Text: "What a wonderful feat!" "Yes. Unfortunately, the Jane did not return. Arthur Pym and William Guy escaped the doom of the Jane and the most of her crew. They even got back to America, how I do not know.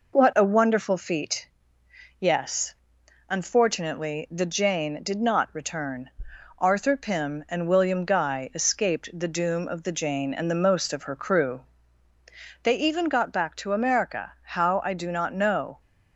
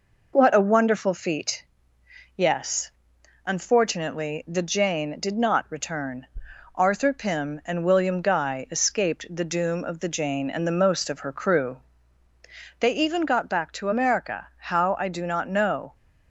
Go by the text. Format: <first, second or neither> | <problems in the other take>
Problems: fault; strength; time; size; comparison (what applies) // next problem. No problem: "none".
neither | none